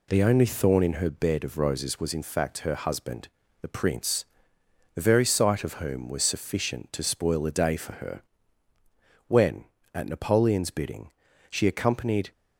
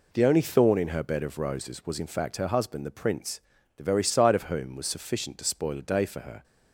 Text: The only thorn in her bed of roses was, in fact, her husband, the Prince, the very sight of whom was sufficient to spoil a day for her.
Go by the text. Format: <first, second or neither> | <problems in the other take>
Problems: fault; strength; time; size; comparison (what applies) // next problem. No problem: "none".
second | goes on to say "When at Napoleon's bidding she accompanied"; strong; from 9.2 s on; 3.0 s long